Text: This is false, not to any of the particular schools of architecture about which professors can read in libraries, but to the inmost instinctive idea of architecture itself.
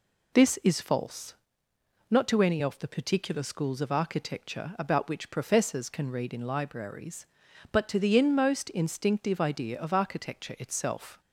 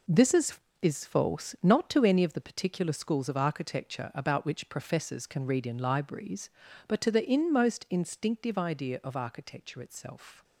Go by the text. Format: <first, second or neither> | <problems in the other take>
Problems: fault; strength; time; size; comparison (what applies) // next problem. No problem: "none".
first | says "is" twice; at 0.8 s